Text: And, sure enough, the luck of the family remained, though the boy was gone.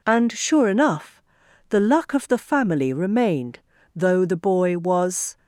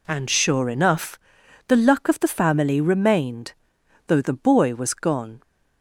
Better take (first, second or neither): second